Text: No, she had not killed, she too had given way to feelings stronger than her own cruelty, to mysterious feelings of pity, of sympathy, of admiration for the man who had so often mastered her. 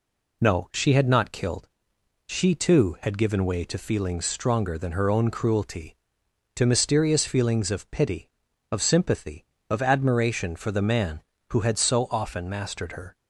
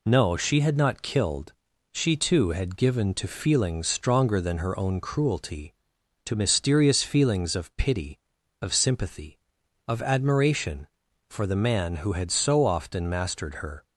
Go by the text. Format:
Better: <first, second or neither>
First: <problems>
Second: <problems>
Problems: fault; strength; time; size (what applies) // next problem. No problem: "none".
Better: first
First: none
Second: skips "way"; at 3.1 s